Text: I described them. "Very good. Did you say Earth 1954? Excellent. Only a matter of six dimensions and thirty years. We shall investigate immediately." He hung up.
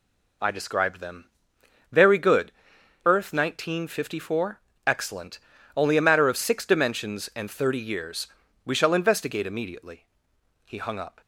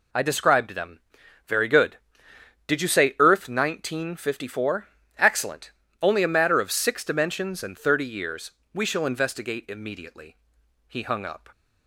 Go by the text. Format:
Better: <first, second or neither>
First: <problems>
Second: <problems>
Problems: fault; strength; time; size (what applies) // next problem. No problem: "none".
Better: second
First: skips "Did you say"; at 2.7 s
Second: none